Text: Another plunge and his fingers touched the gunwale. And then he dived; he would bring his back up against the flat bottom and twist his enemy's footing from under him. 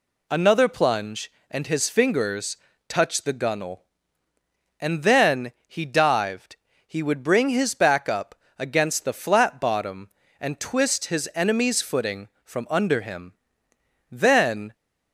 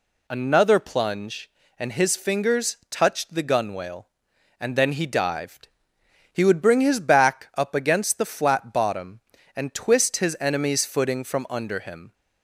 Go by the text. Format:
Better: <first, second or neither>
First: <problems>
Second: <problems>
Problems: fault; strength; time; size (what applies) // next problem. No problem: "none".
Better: second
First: pauses between "fingers" and "touched"; slight; at 2.5 s; 0.32 s long // pauses between "then" and "he"; slight; at 5.5 s; 0.16 s long // pauses between "up" and "against"; slight; at 8.3 s; 0.24 s long // goes on to say "Then"; noticeable; from 14.1 s on; 0.62 s long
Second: none